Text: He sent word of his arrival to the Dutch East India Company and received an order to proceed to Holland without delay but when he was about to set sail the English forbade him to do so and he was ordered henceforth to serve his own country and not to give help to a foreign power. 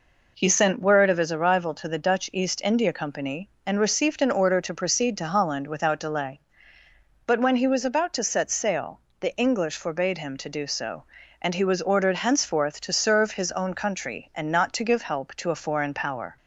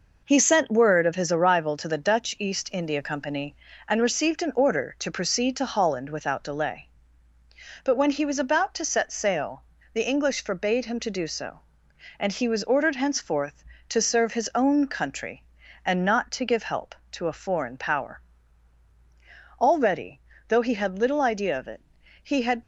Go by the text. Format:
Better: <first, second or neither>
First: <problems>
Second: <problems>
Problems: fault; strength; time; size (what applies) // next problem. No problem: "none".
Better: first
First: pauses between "sail" and "the"; slight; at 8.9 s; 0.22 s long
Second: pauses between "sail" and "the"; slight; at 9.6 s; 0.28 s long // goes on to say "Already though he had little idea of it he had"; strong; from 19.5 s on; 3.0 s long